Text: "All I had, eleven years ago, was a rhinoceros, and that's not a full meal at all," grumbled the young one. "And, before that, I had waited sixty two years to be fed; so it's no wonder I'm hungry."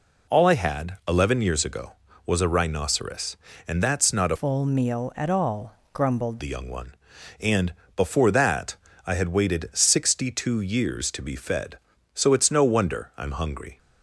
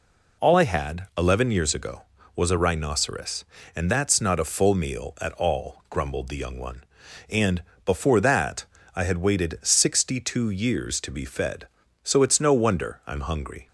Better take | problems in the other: second | changes voice from "full" to "grumbled"; from 4.3 to 6.3 s; 2.0 s long

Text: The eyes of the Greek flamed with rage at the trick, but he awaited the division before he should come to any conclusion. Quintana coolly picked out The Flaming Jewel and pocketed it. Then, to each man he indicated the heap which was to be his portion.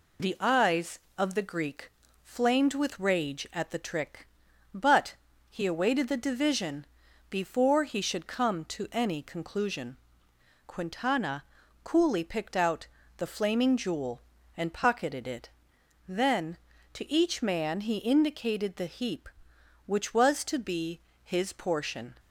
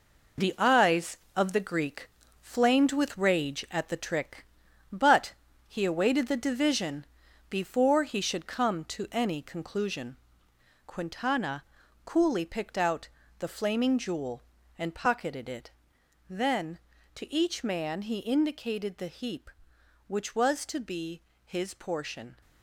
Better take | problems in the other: first | gets quieter; strong; throughout; 8 dB // pauses between "Greek" and "flamed"; slight; at 2.0 s; 0.32 s long; slight in the first // pauses between "but" and "he"; slight; at 5.3 s; 0.34 s long; slight in the first // pauses between "division" and "before"; at 7.0 s; 0.44 s long; also in the first // pauses between "Quintana" and "coolly"; at 11.6 s; 0.41 s long; also in the first // pauses between "out" and "The"; slight; at 13.0 s; 0.28 s long; slight in the first // pauses between "be" and "his"; slight; at 21.2 s; 0.24 s long; slight in the first

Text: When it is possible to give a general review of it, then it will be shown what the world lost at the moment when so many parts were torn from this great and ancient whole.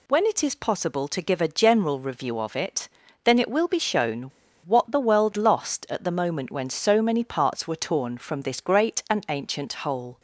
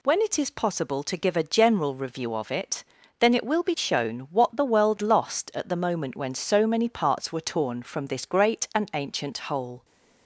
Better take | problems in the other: second | pauses between "shown" and "what"; at 4.2 s; 0.42 s long

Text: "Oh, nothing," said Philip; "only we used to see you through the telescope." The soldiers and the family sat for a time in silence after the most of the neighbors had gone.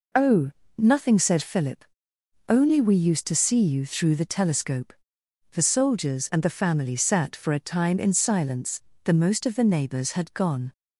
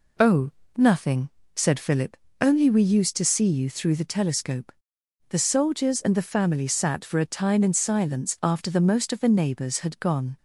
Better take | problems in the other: second | skips "after"; at 8.9 s

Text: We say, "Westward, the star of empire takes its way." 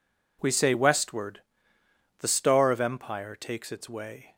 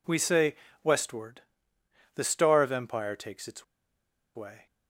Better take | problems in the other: first | pauses between "its" and "way"; noticeable; at 3.6 s; 0.71 s long

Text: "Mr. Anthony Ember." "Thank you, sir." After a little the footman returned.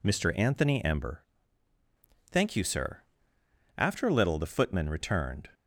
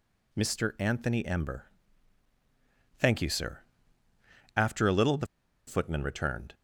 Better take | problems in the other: first | pauses between "the" and "footman"; at 5.2 s; 0.41 s long

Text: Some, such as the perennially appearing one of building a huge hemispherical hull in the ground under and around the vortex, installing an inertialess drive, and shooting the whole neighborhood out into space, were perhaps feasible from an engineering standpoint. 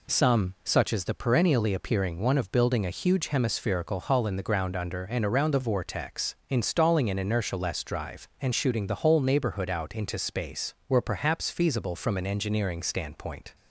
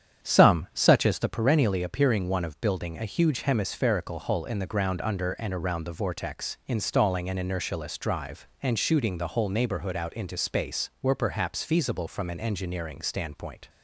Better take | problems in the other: first | starts louder than the rest; strong; until 1.3 s; 8.5 dB

